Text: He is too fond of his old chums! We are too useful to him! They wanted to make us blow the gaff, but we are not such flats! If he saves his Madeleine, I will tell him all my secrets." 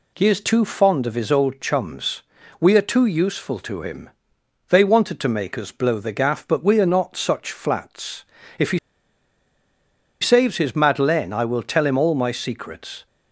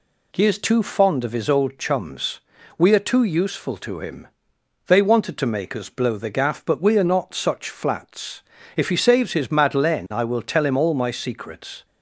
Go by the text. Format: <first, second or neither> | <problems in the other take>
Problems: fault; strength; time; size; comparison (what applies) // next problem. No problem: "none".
second | pauses between "he" and "saves"; strong; at 8.7 s; 1.4 s long